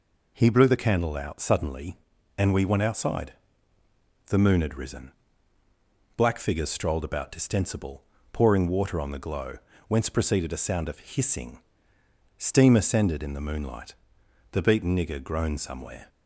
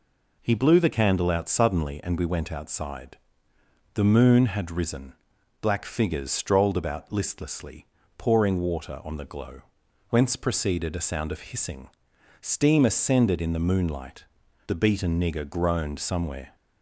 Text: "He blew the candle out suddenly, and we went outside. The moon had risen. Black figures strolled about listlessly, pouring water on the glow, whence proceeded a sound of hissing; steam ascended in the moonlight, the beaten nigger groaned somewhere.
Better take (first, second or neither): second